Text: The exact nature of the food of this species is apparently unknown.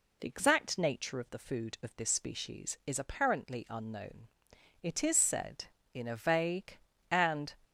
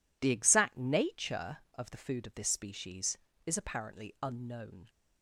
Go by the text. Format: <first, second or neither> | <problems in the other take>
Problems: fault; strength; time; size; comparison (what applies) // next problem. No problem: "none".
second | goes on to say "It is said in a vague and"; strong; from 4.8 s on; 2.7 s long